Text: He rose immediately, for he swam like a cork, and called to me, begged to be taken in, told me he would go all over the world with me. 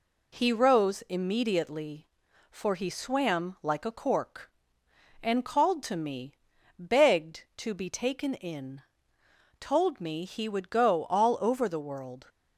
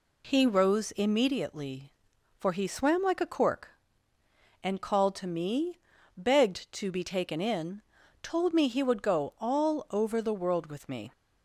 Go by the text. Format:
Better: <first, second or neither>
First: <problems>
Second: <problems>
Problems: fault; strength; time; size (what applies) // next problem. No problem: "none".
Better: second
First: stops before "with me"; at 12.2 s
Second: none